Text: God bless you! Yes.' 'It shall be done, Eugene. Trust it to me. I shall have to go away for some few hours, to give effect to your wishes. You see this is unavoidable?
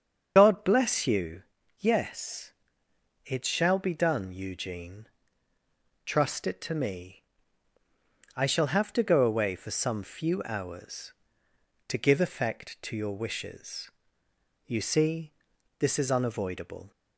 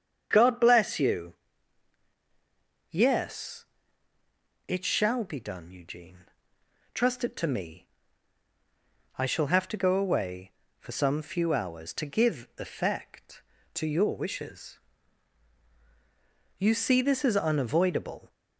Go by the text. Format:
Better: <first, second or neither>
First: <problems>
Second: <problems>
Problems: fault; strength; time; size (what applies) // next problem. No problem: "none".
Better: second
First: loses the start of "God"; at 0.3 s; 55 ms // starts louder than the rest; until 1.3 s; 7 dB // pauses between "see" and "this"; noticeable; at 15.3 s; 0.46 s long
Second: starts louder than the rest; strong; until 1.3 s; 7.5 dB